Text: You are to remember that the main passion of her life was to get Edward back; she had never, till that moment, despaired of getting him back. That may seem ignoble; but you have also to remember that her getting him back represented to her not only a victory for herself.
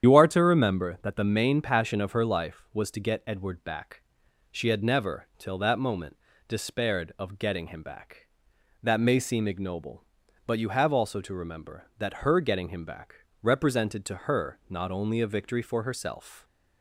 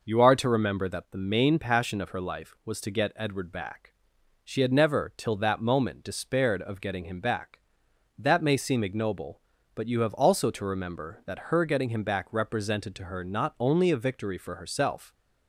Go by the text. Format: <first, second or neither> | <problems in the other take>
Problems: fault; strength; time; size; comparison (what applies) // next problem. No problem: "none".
second | loses the start of "You"; at 0.0 s; 70 ms // starts louder than the rest; strong; until 1.0 s; 9 dB // pauses between "back" and "represented"; slight; at 13.1 s; 0.26 s long